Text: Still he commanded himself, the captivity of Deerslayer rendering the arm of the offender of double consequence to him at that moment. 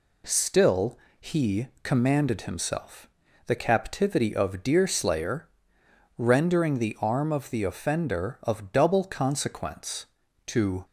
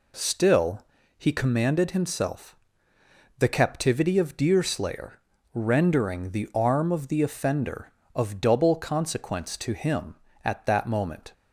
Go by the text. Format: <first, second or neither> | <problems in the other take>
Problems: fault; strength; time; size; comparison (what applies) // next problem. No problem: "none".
second | pauses between "Still" and "he"; slight; at 0.9 s; 0.24 s long; slight in the second // pauses between "he" and "commanded"; slight; at 1.6 s; 0.16 s long // pauses between "Deerslayer" and "rendering"; noticeable; at 5.4 s; 0.70 s long; slight in the second // stops before "him at that moment"; at 10.8 s